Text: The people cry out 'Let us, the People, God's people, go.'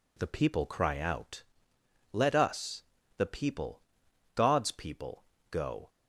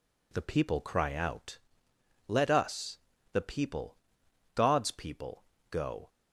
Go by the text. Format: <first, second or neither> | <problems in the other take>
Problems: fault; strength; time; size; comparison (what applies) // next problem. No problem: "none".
neither | pauses between "out" and "Let"; noticeable; the same in both